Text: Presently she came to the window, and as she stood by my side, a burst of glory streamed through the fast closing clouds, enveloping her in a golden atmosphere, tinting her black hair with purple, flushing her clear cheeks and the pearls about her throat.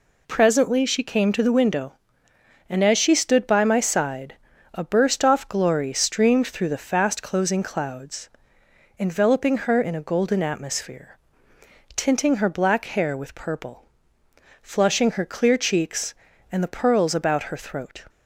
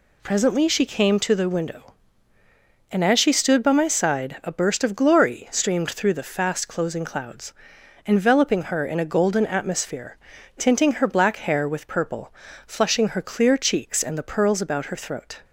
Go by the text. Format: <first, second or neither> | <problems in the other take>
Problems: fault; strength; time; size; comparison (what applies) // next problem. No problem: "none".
second | says "off" for "of"; at 5.2 s